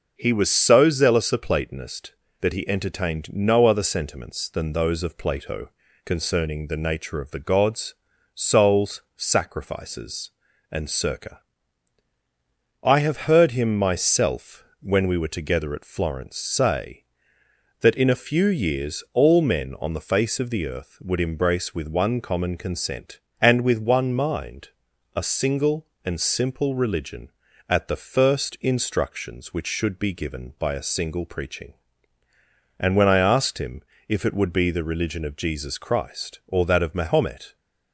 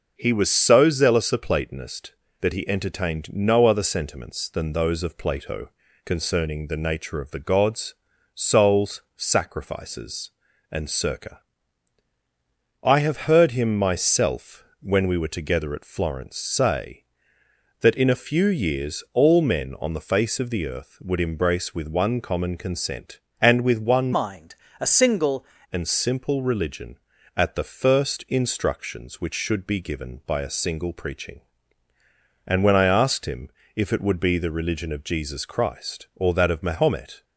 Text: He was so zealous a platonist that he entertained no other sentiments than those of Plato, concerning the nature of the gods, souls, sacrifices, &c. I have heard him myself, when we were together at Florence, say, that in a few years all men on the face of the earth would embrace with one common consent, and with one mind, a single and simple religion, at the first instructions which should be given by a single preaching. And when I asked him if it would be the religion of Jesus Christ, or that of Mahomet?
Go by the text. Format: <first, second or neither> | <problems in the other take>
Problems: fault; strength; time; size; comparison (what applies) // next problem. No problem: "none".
first | changes voice from "mind" to "single"; from 24.1 to 25.4 s; 1.3 s long // pauses between "him" and "if"; slight; at 33.4 s; 0.24 s long; slight in the first